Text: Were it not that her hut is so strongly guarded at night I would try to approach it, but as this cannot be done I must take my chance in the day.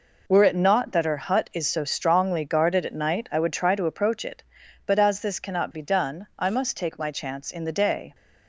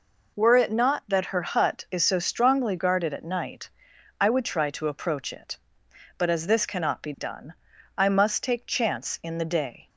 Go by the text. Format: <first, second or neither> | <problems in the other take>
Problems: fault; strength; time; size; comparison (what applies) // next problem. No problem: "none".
first | pauses between "night" and "I"; noticeable; at 3.6 s; 0.50 s long // pauses between "done" and "I"; at 7.5 s; 0.42 s long // skips "my"; at 8.6 s